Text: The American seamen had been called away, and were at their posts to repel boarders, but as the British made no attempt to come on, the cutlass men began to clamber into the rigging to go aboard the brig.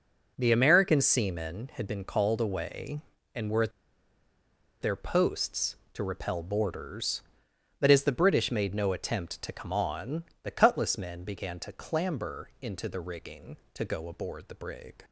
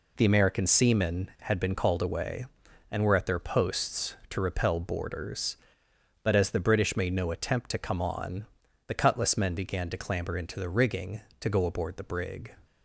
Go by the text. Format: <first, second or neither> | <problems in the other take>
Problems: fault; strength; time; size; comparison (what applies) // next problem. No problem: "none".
second | pauses between "at" and "their"; at 3.7 s; 1.0 s long